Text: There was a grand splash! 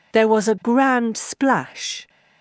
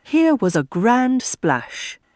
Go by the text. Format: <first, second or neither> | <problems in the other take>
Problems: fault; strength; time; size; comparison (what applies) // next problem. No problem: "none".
first | says "Here" for "There"; at 0.0 s